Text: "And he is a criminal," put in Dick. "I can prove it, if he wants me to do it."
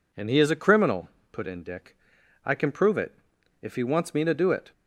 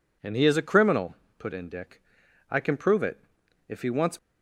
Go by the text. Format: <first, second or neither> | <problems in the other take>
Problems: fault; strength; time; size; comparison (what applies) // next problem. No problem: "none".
first | stops before "me to do it"; at 4.1 s